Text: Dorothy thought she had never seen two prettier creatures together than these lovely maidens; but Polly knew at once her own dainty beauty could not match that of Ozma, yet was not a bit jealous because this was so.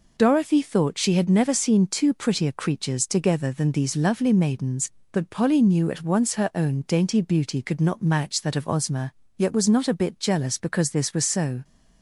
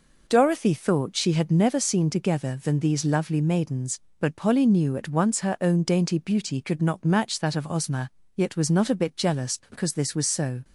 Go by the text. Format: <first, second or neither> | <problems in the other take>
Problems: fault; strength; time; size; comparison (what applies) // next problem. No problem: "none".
first | skips "two prettier creatures"; at 2.0 s